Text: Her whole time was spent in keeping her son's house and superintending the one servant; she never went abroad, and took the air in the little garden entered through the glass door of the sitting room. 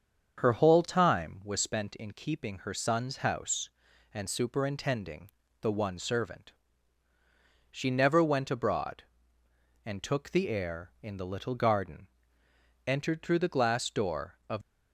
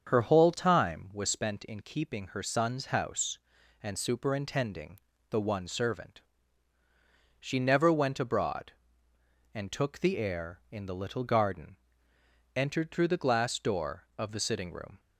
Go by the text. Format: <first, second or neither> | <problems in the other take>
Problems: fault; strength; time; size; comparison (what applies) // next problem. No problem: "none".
second | starts louder than the rest; strong; until 1.3 s; 7 dB; strong in the second // pauses between "superintending" and "the"; slight; at 5.3 s; 0.32 s long; slight in the second // pauses between "garden" and "entered"; noticeable; at 12.0 s; 0.80 s long; noticeable in the second // stops before "the sitting room"; at 14.6 s